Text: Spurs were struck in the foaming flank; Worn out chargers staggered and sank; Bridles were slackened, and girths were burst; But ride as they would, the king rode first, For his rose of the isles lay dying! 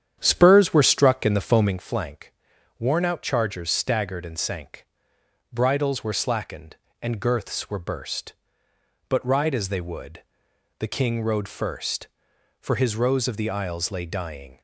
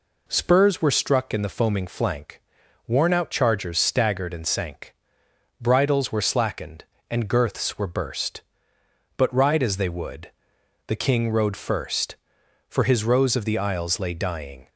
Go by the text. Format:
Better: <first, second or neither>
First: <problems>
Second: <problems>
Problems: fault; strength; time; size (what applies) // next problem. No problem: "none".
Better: second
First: starts louder than the rest; strong; until 1.8 s; 9.5 dB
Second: none